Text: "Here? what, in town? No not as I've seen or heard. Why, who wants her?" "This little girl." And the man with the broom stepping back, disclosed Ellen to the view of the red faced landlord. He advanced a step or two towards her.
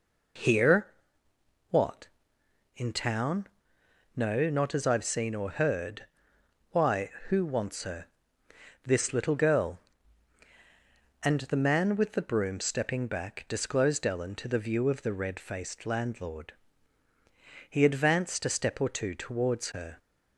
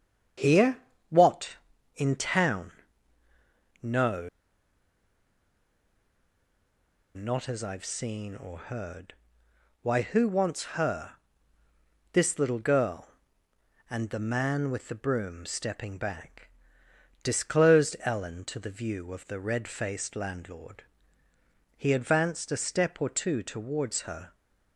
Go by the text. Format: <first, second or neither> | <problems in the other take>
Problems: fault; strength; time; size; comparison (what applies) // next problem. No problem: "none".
first | starts louder than the rest; strong; until 2.1 s; 7.5 dB // pauses between "No" and "not"; strong; at 4.2 s; 2.8 s long